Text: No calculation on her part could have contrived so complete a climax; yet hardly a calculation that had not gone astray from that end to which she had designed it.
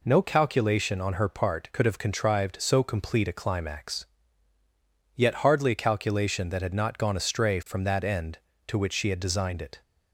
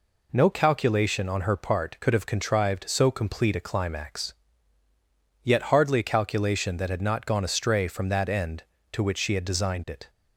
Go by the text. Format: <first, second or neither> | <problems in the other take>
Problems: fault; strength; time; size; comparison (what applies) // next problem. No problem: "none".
neither | none